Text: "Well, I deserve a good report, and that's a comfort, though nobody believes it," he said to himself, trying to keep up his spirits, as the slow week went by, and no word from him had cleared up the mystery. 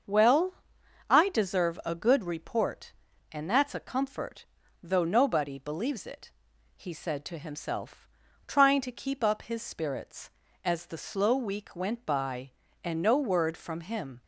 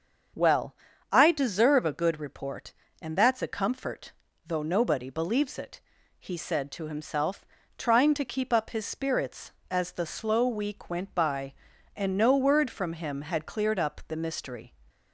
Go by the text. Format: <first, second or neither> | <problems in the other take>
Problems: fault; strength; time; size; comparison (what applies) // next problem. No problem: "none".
second | starts louder than the rest; until 1.6 s; 6.5 dB; strong in the second // stops before "had cleared up the mystery"; at 14.2 s